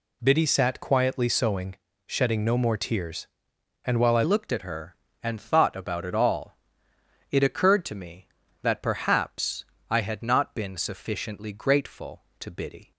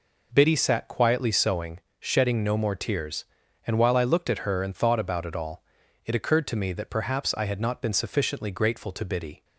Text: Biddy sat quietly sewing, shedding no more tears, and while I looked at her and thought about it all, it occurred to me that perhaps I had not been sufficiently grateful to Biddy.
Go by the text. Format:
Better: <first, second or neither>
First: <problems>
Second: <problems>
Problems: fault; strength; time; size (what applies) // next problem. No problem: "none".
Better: second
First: changes voice at "looked"; from 4.2 s on; 8.7 s long // pauses between "perhaps" and "I"; slight; at 9.6 s; 0.24 s long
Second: none